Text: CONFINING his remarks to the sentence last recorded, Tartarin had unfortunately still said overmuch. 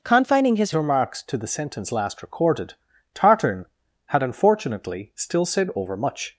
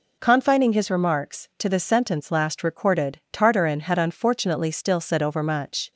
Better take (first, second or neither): second